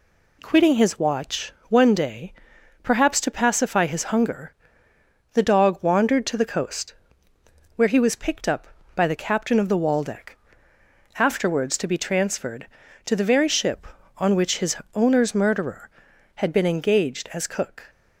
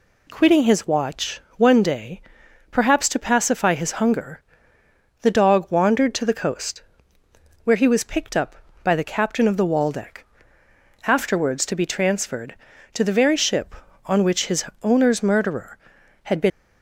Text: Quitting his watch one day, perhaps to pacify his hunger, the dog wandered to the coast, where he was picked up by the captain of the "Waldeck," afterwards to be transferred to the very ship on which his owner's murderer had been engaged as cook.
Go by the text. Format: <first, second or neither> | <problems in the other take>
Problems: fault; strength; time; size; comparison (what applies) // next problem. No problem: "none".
first | pauses between "watch" and "one"; slight; at 1.4 s; 0.16 s long; slight in the first // pauses between "his" and "owner's"; slight; at 14.6 s; 0.18 s long; slight in the first // stops before "engaged as cook"; at 16.5 s